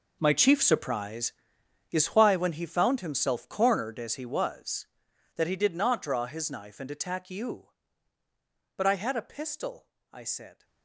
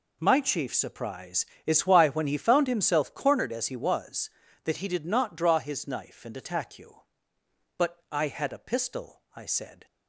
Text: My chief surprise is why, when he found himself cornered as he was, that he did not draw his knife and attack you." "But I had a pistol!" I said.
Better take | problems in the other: second | gets quieter; strong; throughout; 16.5 dB

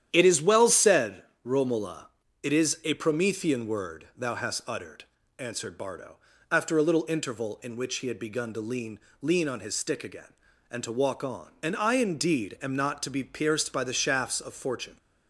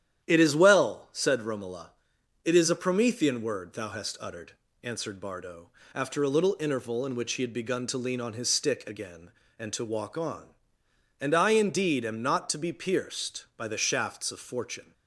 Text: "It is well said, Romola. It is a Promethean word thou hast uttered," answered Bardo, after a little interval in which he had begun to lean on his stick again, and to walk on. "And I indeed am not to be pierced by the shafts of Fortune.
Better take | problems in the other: second | starts louder than the rest; strong; until 1.1 s; 10 dB; strong in the second // says "lean" twice; at 9.2 s

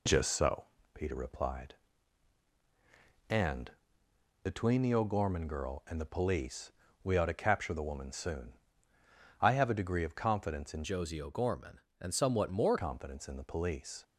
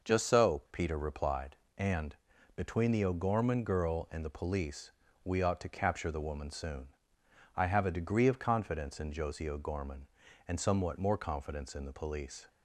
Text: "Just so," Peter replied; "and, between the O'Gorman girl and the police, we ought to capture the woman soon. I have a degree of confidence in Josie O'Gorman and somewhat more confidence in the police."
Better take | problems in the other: second | changes voice from "Josie" to "more"; from 10.8 to 12.7 s; 1.9 s long

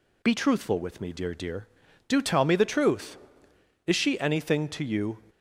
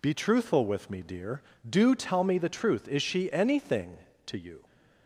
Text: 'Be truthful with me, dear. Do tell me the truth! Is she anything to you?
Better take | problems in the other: second | says "dear" twice; at 1.3 s

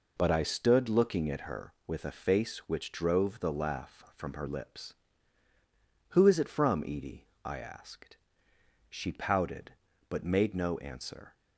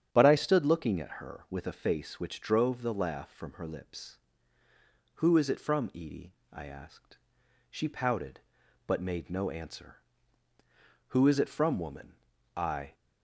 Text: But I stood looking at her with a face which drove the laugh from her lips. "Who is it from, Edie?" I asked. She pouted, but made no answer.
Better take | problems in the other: first | starts louder than the rest; strong; until 1.1 s; 9 dB // goes on to say "Who is it from woman I"; strong; from 11.0 s on; 1.8 s long

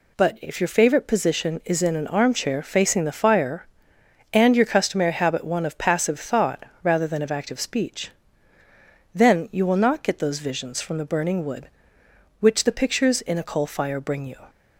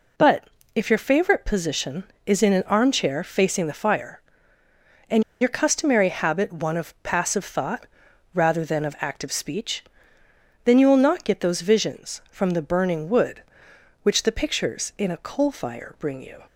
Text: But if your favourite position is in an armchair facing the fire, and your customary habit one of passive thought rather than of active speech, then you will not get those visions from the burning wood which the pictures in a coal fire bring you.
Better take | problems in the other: first | pauses between "But" and "if"; slight; at 0.4 s; 0.30 s long // pauses between "and" and "your"; slight; at 5.2 s; 0.18 s long // pauses between "thought" and "rather"; noticeable; at 7.8 s; 0.46 s long; slight in the first

